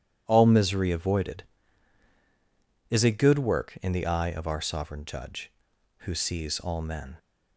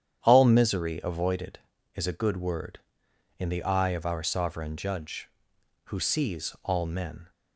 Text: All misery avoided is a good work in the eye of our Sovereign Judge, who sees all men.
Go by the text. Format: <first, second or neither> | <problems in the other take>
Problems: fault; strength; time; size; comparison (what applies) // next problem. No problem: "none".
first | starts louder than the rest; strong; until 1.2 s; 9.5 dB // says "word" for "work"; at 2.3 s